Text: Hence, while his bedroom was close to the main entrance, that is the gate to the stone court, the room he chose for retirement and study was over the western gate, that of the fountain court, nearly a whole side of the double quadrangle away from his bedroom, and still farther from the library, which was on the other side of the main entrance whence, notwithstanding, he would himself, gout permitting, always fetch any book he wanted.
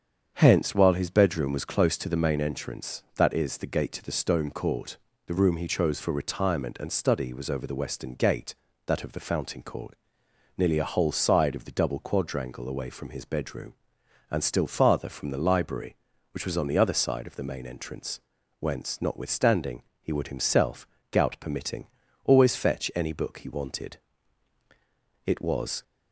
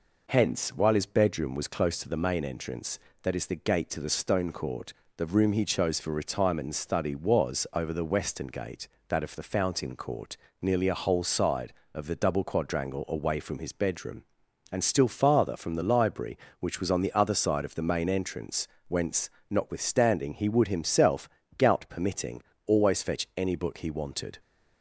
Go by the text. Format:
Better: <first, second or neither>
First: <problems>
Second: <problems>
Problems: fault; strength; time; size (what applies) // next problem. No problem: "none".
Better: second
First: starts louder than the rest; strong; until 1.3 s; 7.5 dB // pauses between "entrance" and "whence"; at 18.1 s; 0.42 s long // goes on to say "It was"; from 25.2 s on; 0.58 s long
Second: pauses between "entrance" and "whence"; slight; at 18.6 s; 0.20 s long